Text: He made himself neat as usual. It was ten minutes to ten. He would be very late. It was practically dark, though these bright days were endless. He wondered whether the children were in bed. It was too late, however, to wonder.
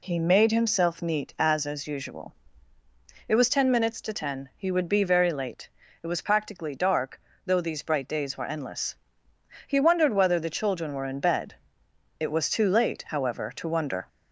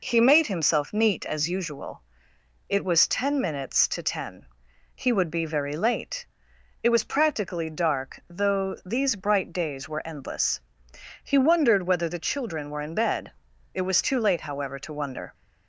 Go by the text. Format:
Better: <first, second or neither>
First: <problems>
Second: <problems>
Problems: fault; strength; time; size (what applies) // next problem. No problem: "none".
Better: second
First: says "as" twice; at 1.6 s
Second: none